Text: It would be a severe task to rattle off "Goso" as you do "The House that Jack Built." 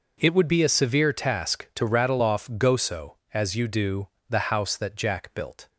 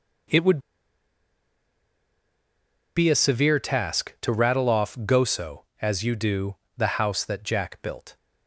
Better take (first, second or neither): first